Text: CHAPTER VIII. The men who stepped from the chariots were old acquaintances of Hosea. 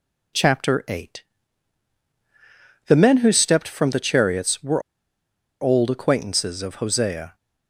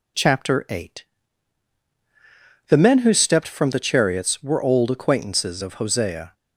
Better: second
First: pauses between "were" and "old"; noticeable; at 4.8 s; 0.80 s long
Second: none

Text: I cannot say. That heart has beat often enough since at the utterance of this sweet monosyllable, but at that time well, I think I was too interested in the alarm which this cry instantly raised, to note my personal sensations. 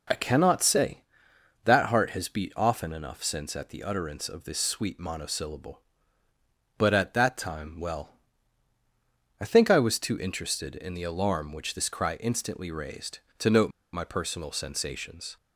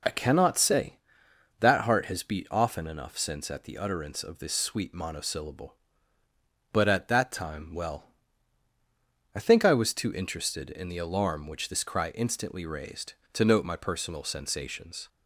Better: second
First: pauses between "note" and "my"; slight; at 13.7 s; 0.22 s long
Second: none

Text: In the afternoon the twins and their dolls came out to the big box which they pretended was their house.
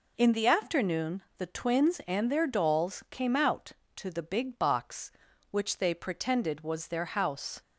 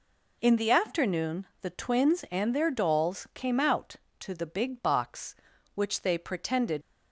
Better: first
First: pauses between "afternoon" and "the"; slight; at 1.2 s; 0.16 s long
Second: pauses between "afternoon" and "the"; slight; at 1.4 s; 0.16 s long // stops before "was their house"; at 6.8 s

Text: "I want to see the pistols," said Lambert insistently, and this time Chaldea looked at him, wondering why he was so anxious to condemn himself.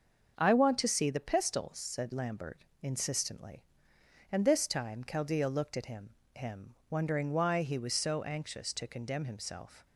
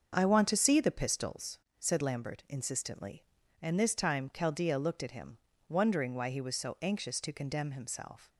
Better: second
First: starts louder than the rest; until 1.3 s; 6.5 dB // pauses between "Lambert" and "insistently"; slight; at 2.6 s; 0.16 s long // says "him" twice; at 6.3 s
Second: starts louder than the rest; until 1.2 s; 6.5 dB

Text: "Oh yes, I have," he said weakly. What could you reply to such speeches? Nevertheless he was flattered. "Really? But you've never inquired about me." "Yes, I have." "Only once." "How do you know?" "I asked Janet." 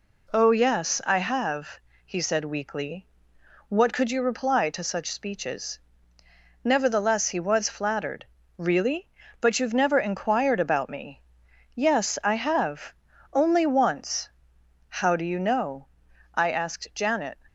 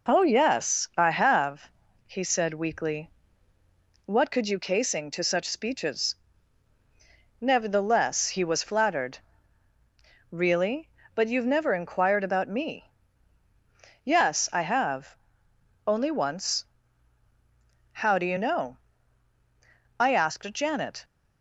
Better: first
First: none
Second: says "casing" for "reply"; at 4.5 s

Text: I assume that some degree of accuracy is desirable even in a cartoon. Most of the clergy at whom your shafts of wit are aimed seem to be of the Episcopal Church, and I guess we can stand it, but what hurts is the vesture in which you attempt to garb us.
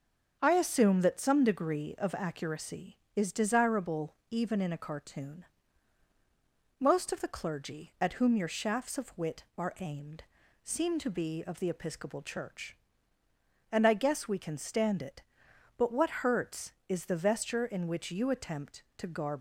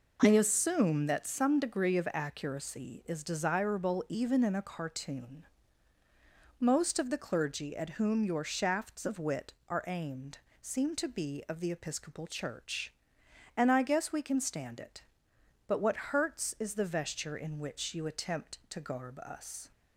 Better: second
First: starts louder than the rest; until 1.4 s; 7 dB // pauses between "desirable" and "even"; slight; at 4.1 s; 0.16 s long // pauses between "aimed" and "seem"; at 10.2 s; 0.40 s long // stops before "us"; at 19.3 s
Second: pauses between "aimed" and "seem"; slight; at 10.3 s; 0.24 s long

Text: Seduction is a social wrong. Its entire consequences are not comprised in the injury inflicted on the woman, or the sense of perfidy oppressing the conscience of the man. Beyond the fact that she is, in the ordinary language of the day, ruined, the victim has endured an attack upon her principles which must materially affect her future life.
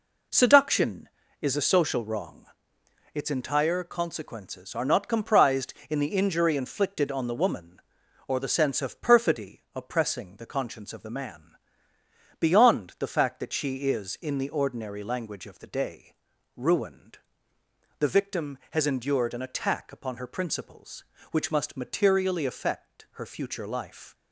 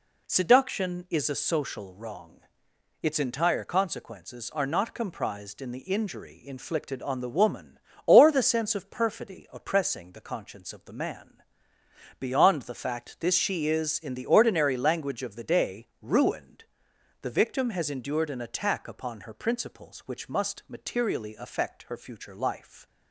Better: first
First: none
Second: says "this" for "that"; at 13.1 s

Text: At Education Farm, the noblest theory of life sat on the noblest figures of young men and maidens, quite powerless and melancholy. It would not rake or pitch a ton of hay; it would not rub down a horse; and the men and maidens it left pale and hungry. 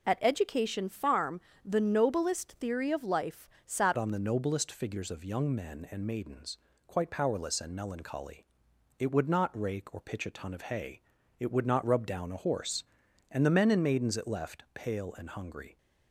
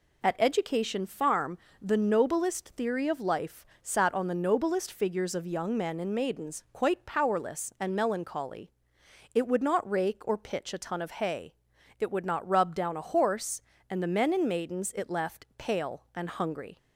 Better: second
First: pauses between "life" and "sat"; slight; at 3.4 s; 0.16 s long // changes voice at "on"; from 3.9 s on; 11.8 s long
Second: pauses between "life" and "sat"; slight; at 3.6 s; 0.16 s long

